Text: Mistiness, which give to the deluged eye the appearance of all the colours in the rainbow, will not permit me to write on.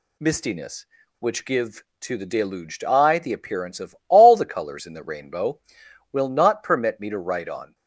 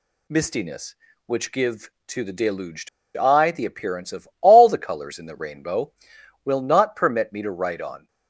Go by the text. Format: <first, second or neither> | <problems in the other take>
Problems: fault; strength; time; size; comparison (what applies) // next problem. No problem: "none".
first | pauses between "deluged" and "eye"; slight; at 2.8 s; 0.28 s long